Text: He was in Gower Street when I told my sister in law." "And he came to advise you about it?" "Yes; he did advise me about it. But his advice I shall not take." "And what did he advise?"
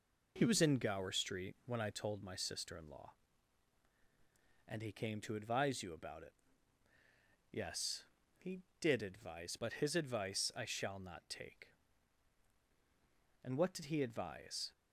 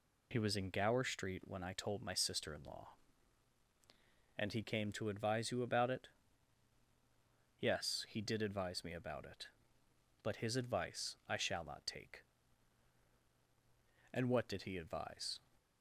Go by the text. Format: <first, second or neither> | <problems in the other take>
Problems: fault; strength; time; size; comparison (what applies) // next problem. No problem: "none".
second | skips "me about it"; at 9.5 s